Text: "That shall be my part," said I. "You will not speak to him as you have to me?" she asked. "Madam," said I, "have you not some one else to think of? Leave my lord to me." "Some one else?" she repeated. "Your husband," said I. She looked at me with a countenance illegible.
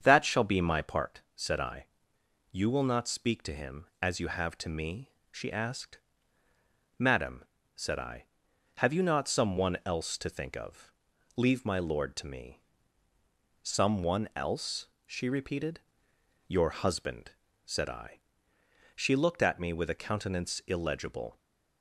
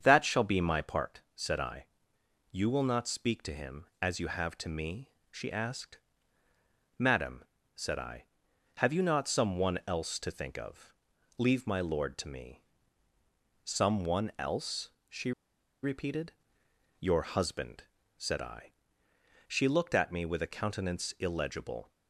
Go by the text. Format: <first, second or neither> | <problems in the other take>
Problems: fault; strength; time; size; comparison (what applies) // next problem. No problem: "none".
first | starts louder than the rest; strong; until 1.0 s; 7.5 dB; strong in the first // pauses between "she" and "repeated"; noticeable; at 15.3 s; 0.51 s long